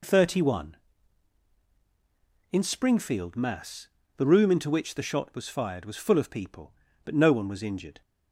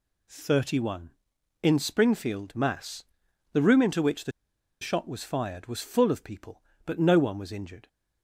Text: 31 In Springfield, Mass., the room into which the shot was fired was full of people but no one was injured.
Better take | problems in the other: first | pauses between "the" and "shot"; noticeable; at 4.3 s; 0.50 s long

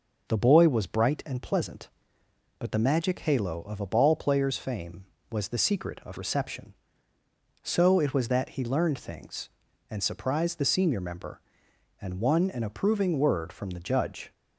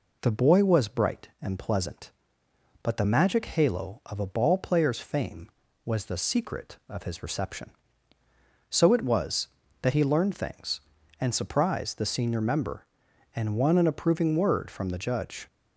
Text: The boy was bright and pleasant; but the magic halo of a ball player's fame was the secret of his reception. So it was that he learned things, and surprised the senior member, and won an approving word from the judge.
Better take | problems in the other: second | skips "his"; at 6.1 s

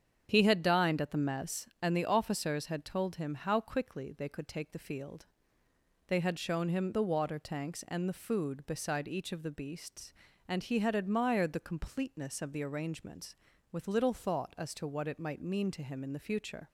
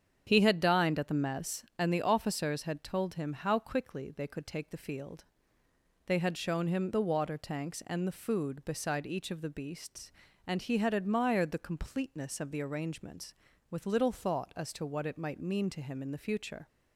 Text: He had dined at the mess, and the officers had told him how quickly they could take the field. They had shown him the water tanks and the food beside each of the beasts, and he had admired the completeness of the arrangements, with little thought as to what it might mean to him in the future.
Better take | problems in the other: neither | starts louder than the rest; strong; the same in both

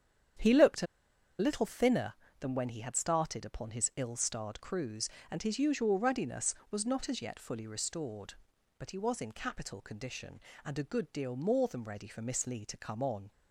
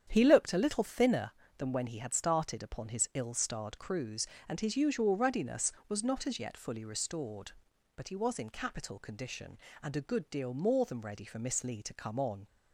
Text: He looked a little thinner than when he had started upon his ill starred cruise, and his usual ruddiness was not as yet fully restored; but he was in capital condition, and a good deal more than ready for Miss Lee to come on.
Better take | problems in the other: second | starts louder than the rest; strong; until 1.9 s; 8.5 dB; strong in the second // pauses between "a" and "little"; noticeable; at 0.8 s; 0.54 s long

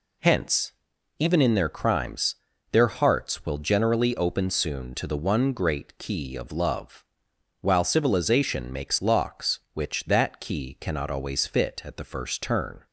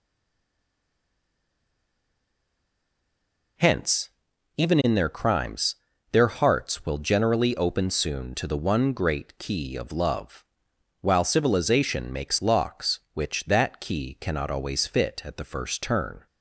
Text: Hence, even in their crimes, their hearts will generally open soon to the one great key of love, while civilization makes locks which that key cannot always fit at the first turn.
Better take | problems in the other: first | stays silent before the first word; strong; until 3.5 s; 3.5 s long

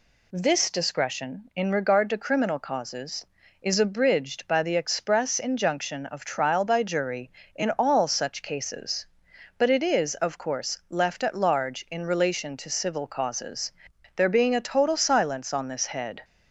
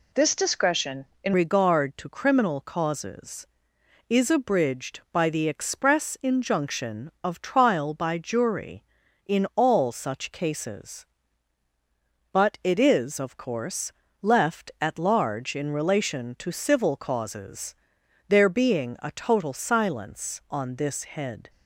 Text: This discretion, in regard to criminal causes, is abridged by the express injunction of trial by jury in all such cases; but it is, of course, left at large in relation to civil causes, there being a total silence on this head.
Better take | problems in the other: first | changes voice at "regard"; from 1.3 s on; 20.1 s long

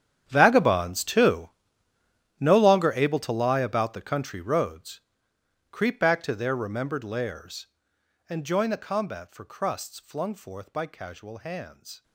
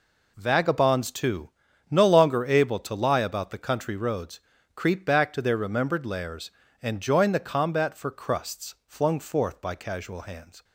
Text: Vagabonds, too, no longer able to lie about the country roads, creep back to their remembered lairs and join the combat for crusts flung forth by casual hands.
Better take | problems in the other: second | gets quieter; strong; throughout; 18.5 dB

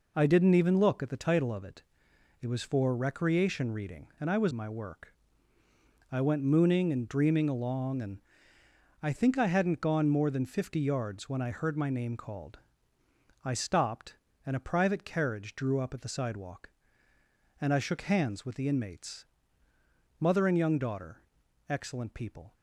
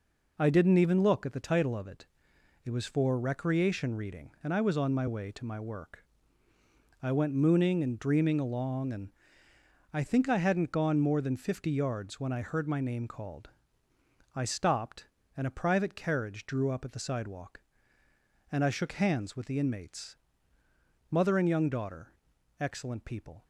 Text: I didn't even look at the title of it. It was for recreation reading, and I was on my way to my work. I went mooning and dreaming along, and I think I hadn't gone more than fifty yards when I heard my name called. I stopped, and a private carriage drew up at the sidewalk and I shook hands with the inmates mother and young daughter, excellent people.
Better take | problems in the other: second | skips "on my way to"; at 4.5 s // pauses between "and" and "I"; noticeable; at 8.1 s; 0.82 s long; noticeable in the second // pauses between "inmates" and "mother"; noticeable; at 19.2 s; 0.96 s long; noticeable in the second

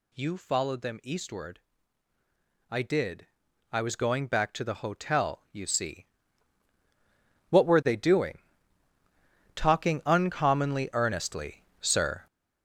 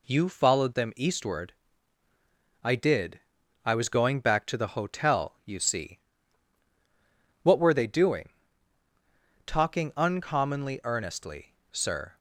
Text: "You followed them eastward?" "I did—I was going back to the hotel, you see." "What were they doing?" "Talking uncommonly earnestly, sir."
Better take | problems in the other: second | gets louder; strong; throughout; 7.5 dB

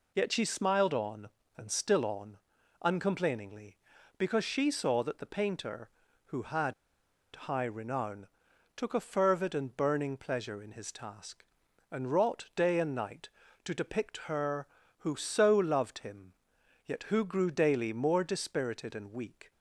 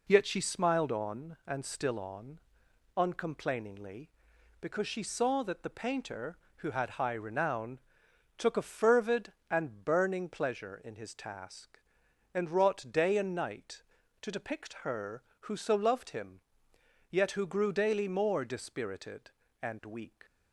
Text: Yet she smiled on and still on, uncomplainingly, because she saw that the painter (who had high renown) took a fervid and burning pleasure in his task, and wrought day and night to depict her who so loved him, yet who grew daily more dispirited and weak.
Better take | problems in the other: second | pauses between "had" and "high"; noticeable; at 6.7 s; 0.60 s long

